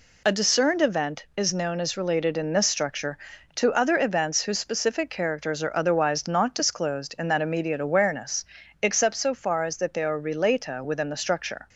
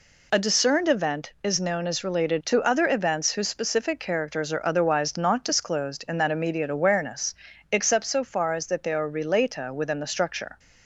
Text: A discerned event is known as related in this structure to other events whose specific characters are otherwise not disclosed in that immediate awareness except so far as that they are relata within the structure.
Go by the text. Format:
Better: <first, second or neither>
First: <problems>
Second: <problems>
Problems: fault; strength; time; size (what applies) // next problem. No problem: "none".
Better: first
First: pauses between "awareness" and "except"; at 8.4 s; 0.38 s long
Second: skips "in this structure"; at 2.4 s // pauses between "awareness" and "except"; at 7.3 s; 0.38 s long